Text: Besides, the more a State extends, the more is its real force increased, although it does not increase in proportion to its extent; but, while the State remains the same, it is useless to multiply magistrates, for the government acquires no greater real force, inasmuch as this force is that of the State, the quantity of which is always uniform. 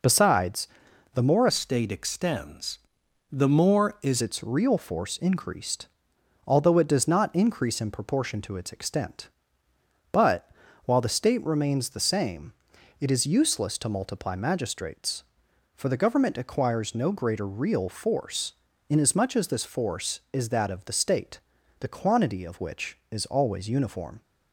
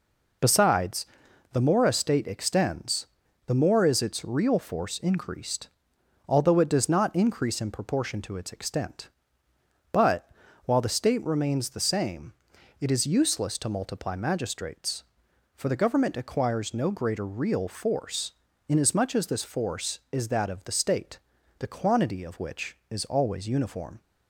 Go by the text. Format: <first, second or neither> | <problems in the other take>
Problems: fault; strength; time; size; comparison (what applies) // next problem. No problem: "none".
second | changes voice from "a" to "is"; from 1.4 to 4.2 s; 2.8 s long